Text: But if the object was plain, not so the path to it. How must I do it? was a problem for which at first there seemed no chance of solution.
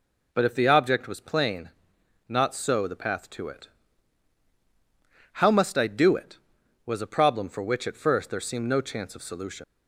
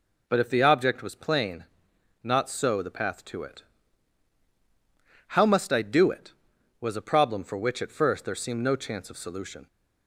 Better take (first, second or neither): second